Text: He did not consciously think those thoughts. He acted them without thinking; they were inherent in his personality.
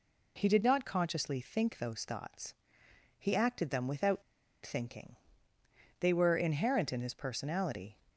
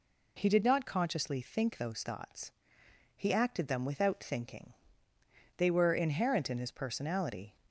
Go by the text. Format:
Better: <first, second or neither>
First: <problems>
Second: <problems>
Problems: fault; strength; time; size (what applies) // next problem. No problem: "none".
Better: second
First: pauses between "without" and "thinking"; at 4.2 s; 0.40 s long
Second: none